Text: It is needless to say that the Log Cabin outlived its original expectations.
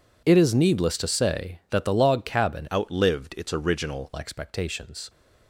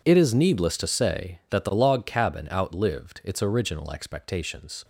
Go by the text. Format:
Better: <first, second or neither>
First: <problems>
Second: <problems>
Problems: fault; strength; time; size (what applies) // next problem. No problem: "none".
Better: second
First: changes voice from "outlived" to "original"; from 2.7 to 4.1 s; 1.4 s long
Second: none